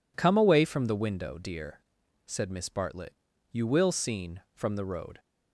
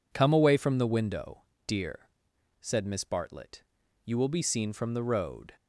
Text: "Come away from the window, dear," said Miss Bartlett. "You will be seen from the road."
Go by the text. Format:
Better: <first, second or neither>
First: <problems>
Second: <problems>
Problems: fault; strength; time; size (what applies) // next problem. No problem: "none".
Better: second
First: skips "be"; at 3.9 s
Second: none